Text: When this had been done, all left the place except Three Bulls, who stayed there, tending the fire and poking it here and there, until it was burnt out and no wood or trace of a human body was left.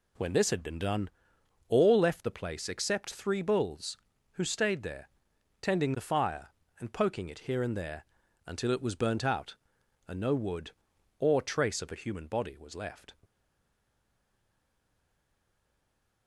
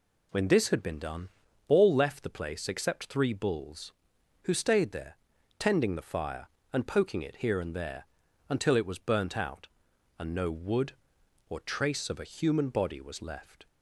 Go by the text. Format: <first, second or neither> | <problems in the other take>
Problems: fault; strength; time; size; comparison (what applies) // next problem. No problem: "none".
second | stays silent after the last word; strong; from 13.2 s on; 3.0 s long